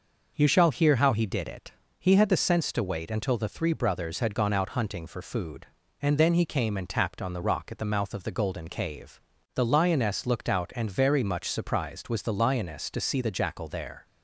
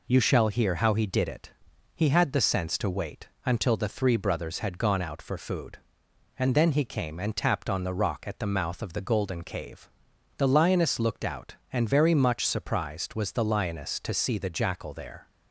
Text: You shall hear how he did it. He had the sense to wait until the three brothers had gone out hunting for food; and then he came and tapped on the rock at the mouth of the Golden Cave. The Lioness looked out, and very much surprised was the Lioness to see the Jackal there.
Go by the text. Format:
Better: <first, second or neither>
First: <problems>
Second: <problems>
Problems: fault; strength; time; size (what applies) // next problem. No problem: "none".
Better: first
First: none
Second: pauses between "wait" and "until"; slight; at 3.2 s; 0.16 s long // skips "hunting"; at 5.2 s